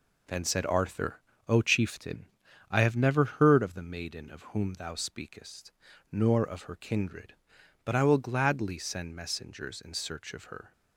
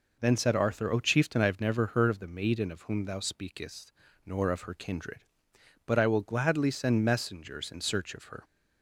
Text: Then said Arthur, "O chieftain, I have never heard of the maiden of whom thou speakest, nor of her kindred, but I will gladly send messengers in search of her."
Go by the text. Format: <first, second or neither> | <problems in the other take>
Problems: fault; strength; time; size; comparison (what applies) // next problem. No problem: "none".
neither | none